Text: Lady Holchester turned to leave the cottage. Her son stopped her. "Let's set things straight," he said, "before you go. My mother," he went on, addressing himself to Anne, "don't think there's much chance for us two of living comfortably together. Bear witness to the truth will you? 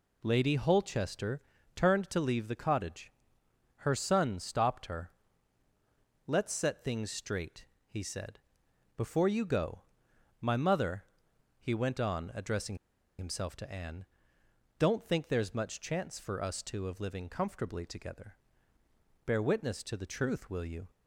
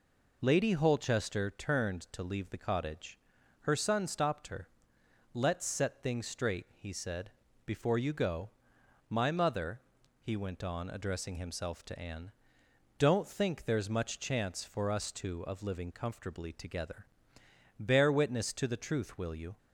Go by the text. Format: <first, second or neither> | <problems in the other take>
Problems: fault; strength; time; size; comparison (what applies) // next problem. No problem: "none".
second | pauses between "Holchester" and "turned"; slight; at 1.4 s; 0.36 s long // pauses between "addressing" and "himself"; at 12.7 s; 0.44 s long